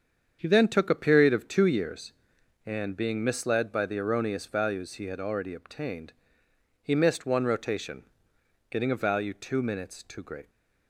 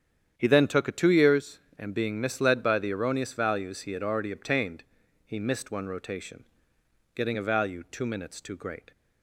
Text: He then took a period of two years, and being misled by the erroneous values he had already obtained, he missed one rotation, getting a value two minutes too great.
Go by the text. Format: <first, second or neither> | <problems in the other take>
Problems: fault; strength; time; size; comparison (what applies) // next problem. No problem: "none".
first | starts louder than the rest; strong; until 1.3 s; 9 dB; strong in the first // skips "period of"; at 0.9 s